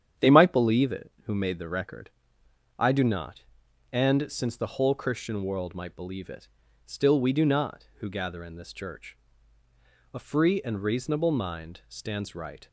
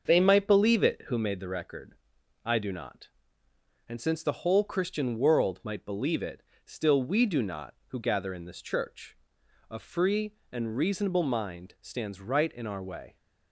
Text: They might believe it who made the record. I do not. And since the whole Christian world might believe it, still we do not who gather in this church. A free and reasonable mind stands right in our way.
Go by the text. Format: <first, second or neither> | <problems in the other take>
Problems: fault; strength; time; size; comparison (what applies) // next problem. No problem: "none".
second | starts louder than the rest; strong; until 1.3 s; 9 dB; also in the second // stops before "in our way"; at 12.6 s